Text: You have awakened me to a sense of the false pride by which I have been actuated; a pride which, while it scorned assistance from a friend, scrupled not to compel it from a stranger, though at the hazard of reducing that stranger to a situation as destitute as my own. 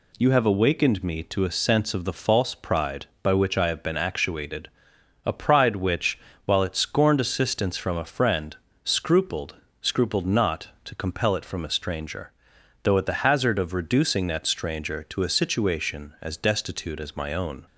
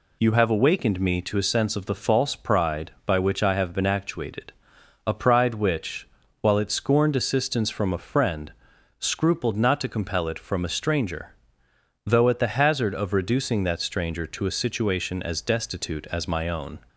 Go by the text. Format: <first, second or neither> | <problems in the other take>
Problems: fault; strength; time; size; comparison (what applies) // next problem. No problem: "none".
second | says "scrupled" twice; at 9.8 s